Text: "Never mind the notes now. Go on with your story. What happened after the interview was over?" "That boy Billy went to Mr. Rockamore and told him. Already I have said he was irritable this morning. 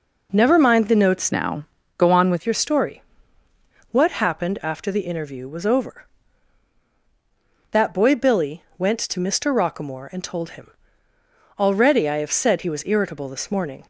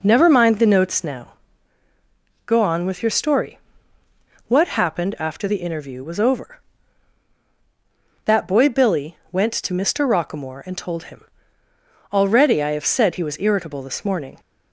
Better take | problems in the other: second | changes voice from "now" to "with"; from 1.3 to 2.4 s; 1.1 s long // pauses between "Billy" and "went"; slight; at 8.6 s; 0.16 s long; slight in the second

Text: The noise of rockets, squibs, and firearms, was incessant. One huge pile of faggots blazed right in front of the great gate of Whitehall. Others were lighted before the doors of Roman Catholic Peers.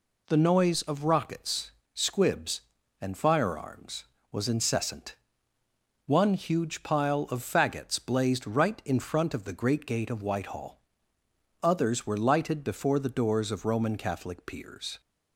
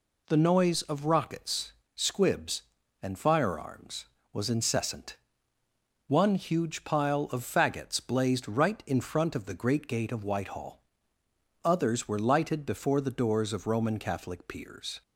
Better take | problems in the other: neither | none

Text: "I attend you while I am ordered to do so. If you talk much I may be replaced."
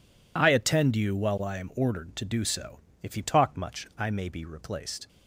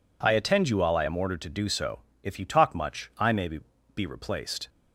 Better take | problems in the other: first | says "be" twice; at 3.9 s

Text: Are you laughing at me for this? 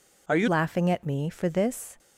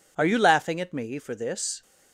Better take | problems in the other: second | changes voice at "laughing"; from 0.4 s on; 1.5 s long

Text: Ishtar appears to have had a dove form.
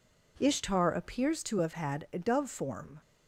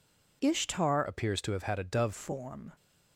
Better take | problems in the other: first | changes voice from "appears" to "dove"; from 1.0 to 2.1 s; 1.1 s long

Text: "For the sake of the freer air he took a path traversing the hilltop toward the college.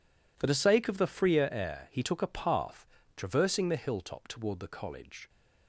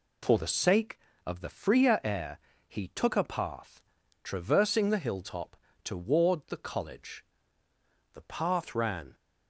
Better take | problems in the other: first | pauses between "air" and "he"; slight; at 2.3 s; 0.28 s long // pauses between "path" and "traversing"; at 3.8 s; 0.42 s long; slight in the first // pauses between "hilltop" and "toward"; slight; at 5.5 s; 0.30 s long // goes on to say "The path ran"; noticeable; from 8.1 s on; 1.0 s long

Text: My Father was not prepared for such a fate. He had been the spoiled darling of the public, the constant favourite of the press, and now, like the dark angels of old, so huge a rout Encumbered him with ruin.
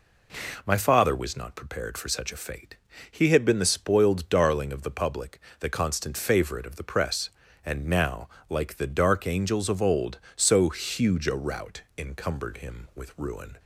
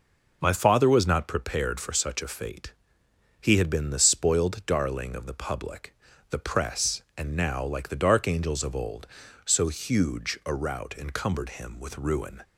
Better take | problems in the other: first | skips "the constant favourite of"; at 6.1 s

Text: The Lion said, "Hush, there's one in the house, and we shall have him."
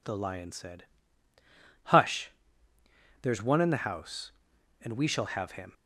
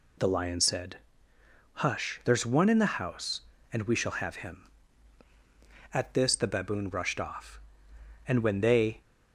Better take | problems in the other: first | goes on to say "At this the Baboon rushed off and when they"; strong; from 5.9 s on; 3.0 s long

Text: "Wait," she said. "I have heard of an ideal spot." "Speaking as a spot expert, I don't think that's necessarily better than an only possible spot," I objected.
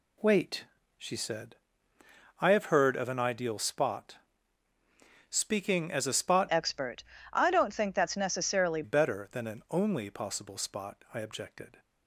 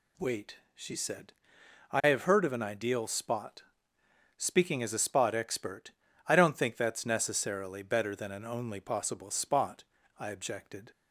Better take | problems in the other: second | changes voice from "expert" to "necessarily"; from 6.4 to 8.8 s; 2.4 s long

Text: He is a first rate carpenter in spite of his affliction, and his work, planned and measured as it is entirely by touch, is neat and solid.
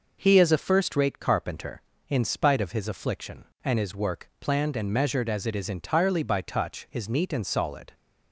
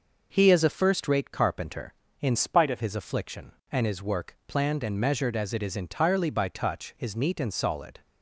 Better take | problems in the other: first | changes voice from "spite" to "of"; from 2.3 to 2.8 s; 0.5 s long

